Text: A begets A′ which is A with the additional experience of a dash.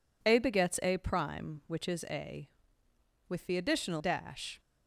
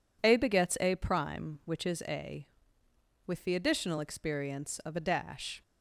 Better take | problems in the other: second | skips "experience of a"; at 3.9 s

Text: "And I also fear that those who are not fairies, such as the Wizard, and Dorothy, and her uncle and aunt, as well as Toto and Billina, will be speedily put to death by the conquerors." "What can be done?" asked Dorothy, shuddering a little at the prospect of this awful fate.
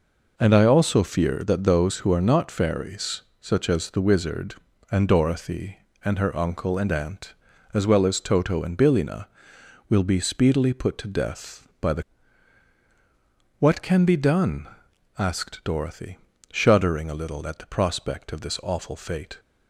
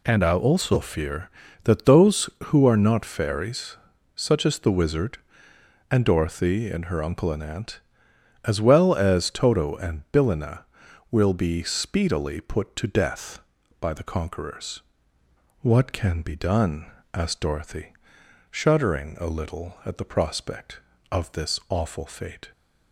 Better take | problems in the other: second | skips "conquerors"; at 12.8 s

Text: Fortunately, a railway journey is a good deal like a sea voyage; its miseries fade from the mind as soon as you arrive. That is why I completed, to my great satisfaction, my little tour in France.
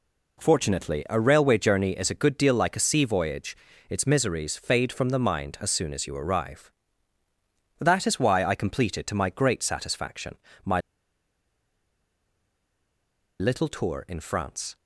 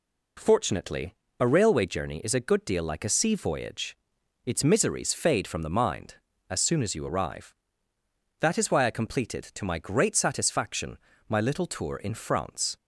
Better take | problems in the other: second | pauses between "my" and "little"; strong; at 10.8 s; 2.5 s long

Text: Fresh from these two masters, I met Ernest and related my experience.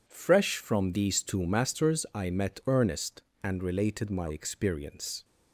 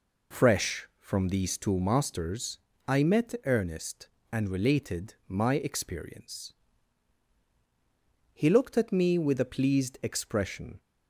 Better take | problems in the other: first | goes on to say "He looked at me with a pleased expression"; strong; from 8.3 s on; 2.4 s long

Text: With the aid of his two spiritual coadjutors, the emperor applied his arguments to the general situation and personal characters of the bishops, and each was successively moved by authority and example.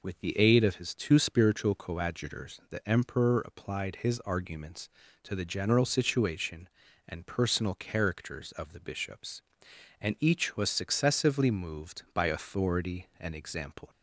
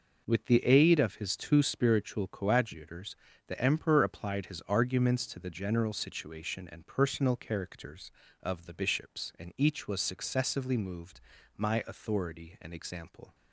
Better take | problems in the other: first | says "my" for "by"; at 11.5 s

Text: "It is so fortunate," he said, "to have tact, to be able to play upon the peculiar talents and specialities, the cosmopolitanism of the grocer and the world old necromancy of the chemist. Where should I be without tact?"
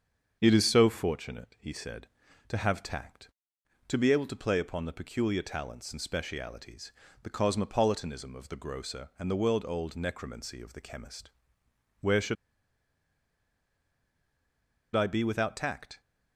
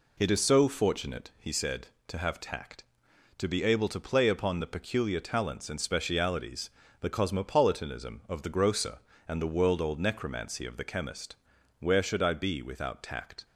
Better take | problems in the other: second | starts louder than the rest; until 1.4 s; 7 dB // pauses between "should" and "I"; strong; at 12.3 s; 2.6 s long

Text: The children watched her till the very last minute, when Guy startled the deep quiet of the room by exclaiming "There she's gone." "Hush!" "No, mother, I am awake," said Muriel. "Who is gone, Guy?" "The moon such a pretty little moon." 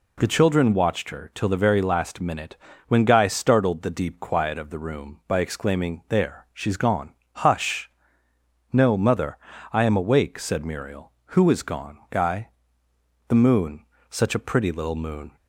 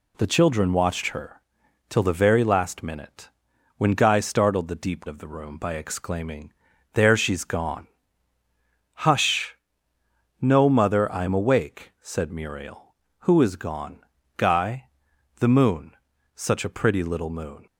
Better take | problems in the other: first | pauses between "her" and "till"; noticeable; at 1.4 s; 0.48 s long // skips "quiet"; at 5.0 s // pauses between "exclaiming" and "There"; at 6.5 s; 0.40 s long // pauses between "moon" and "such"; at 15.9 s; 0.40 s long; slight in the first

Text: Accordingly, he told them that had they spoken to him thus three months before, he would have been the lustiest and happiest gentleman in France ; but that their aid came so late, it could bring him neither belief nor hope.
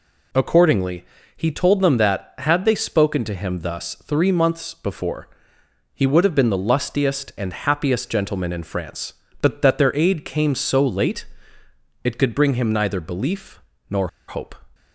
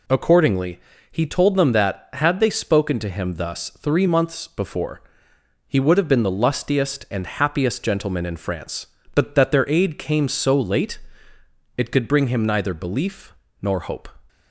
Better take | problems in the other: second | pauses between "belief" and "nor"; slight; at 13.5 s; 0.30 s long; slight in the second // pauses between "nor" and "hope"; slight; at 14.0 s; 0.21 s long

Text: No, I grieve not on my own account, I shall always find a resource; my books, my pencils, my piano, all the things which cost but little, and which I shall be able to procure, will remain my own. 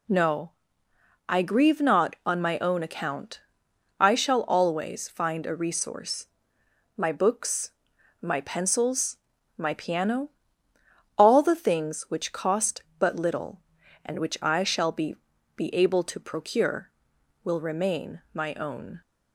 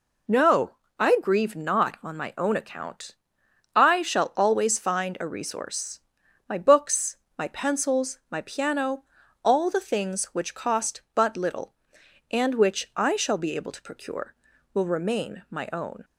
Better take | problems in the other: second | says "be" twice; at 15.5 s

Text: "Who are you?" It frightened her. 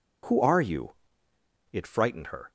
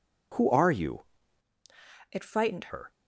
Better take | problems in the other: first | changes voice from "It" to "frightened"; from 2.0 to 2.7 s; 0.7 s long

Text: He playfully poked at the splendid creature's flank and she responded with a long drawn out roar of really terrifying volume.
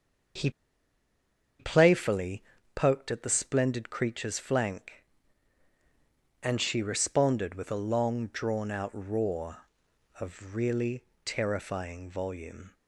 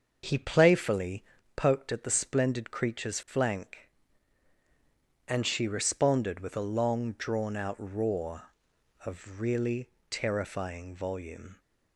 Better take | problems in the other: second | starts louder than the rest; until 2.7 s; 6.5 dB; also in the second // pauses between "He" and "playfully"; at 0.5 s; 1.0 s long // pauses between "playfully" and "poked"; slight; at 2.4 s; 0.32 s long; slight in the second // pauses between "really" and "terrifying"; slight; at 11.0 s; 0.22 s long; slight in the second

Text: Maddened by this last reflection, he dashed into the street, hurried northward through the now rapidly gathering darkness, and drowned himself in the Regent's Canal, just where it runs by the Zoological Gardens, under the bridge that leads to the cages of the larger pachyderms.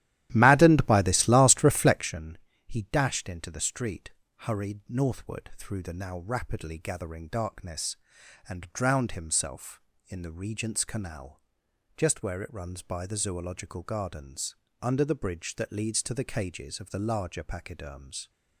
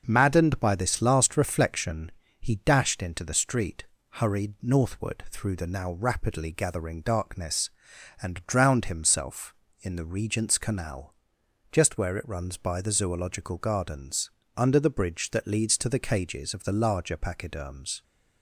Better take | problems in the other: second | starts louder than the rest; strong; until 2.1 s; 13 dB

